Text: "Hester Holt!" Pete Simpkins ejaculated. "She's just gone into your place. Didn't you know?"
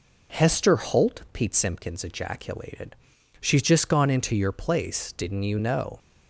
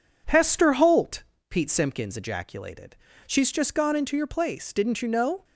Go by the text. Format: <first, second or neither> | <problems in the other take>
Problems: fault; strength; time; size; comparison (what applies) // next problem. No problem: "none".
neither | none